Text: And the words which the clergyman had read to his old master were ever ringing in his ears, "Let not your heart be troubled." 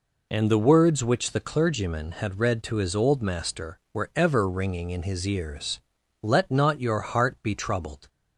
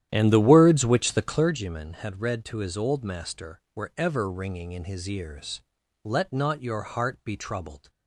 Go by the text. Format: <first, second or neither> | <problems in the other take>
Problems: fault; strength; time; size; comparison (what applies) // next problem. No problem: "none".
first | starts louder than the rest; strong; until 1.6 s; 11 dB